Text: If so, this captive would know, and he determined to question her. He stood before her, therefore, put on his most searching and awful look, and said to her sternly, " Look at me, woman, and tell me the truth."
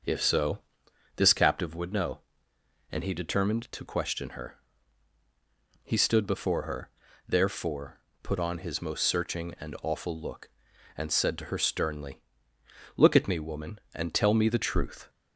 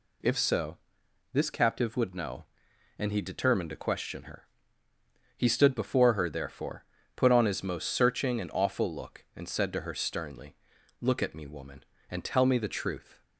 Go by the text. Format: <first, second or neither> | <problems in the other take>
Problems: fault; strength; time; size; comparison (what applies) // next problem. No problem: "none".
neither | none